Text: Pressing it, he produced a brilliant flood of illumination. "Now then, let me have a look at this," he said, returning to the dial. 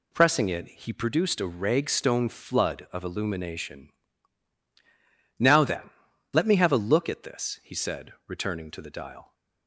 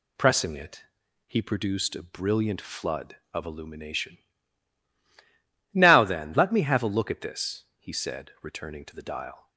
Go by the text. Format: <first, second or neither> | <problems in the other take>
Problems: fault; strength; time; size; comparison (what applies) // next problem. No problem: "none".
second | says "ragstone" for "brilliant"; at 1.4 s